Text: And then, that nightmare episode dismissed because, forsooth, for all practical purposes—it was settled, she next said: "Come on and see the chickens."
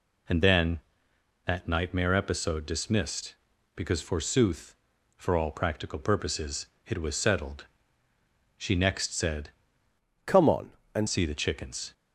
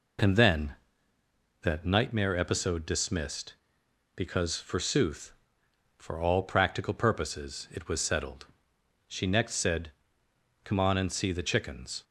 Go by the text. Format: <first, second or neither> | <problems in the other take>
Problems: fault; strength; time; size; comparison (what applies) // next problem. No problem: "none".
second | changes voice from "Come" to "and"; from 10.2 to 11.0 s; 0.8 s long